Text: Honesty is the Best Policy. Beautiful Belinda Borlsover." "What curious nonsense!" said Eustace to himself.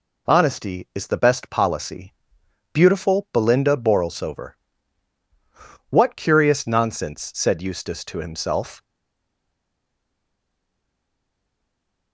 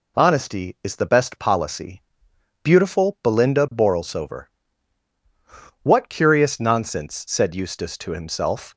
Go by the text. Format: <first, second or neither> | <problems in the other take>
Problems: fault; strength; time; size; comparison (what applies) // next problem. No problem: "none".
second | stays silent after the last word; strong; from 8.8 s on; 3.3 s long